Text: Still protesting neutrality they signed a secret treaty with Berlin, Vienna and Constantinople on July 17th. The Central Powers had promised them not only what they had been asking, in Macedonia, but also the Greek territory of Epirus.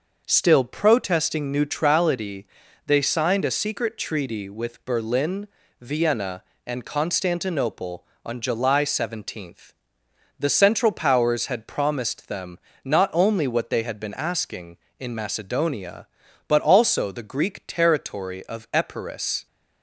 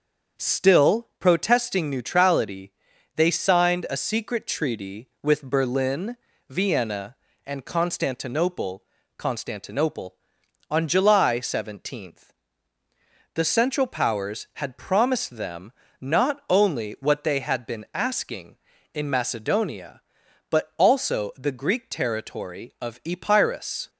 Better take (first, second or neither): first